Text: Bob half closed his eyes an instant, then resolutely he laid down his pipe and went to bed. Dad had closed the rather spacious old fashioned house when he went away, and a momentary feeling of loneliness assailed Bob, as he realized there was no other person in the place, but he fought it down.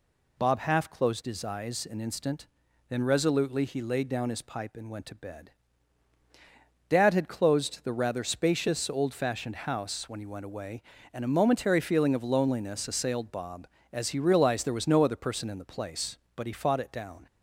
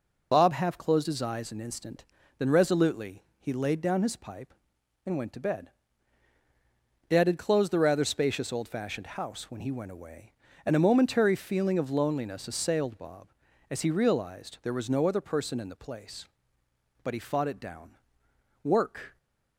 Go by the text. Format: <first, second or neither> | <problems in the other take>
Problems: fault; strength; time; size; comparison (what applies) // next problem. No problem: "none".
first | pauses between "resolutely" and "he"; slight; at 3.2 s; 0.16 s long // goes on to say "Work"; from 18.6 s on; 0.54 s long